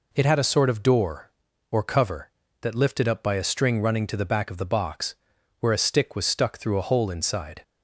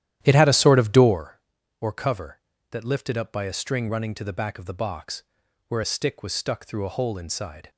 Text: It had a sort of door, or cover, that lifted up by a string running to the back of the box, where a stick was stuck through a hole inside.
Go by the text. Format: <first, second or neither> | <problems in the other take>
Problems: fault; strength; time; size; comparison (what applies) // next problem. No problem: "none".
first | starts louder than the rest; strong; until 1.2 s; 12 dB